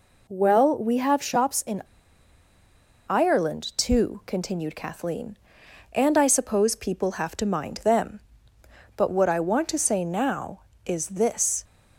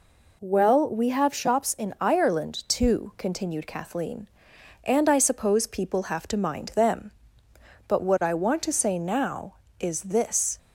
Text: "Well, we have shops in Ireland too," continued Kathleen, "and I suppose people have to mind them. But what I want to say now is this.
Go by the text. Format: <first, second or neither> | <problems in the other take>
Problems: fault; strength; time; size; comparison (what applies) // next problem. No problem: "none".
second | pauses between "in" and "Ireland"; at 1.8 s; 1.2 s long